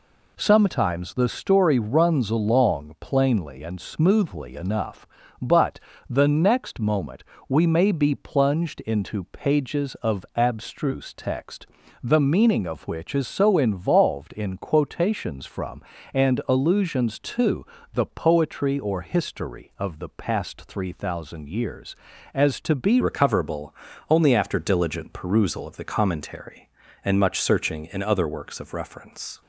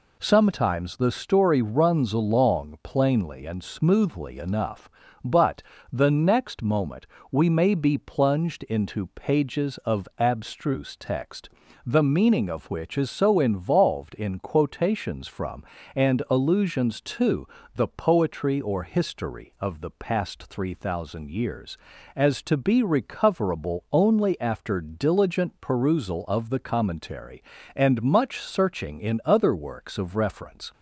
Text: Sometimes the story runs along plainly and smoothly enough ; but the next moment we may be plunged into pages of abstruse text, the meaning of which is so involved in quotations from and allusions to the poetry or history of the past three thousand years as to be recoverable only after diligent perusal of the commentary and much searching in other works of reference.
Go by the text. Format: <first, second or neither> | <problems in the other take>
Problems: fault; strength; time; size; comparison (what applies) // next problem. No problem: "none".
second | pauses between "but" and "the"; slight; at 5.8 s; 0.30 s long; slight in the second // pauses between "moment" and "we"; slight; at 7.2 s; 0.24 s long; slight in the second // pauses between "to" and "the"; slight; at 17.6 s; 0.28 s long; slight in the second // changes voice at "recoverable"; from 23.0 s on; 6.4 s long // pauses between "recoverable" and "only"; slight; at 23.7 s; 0.36 s long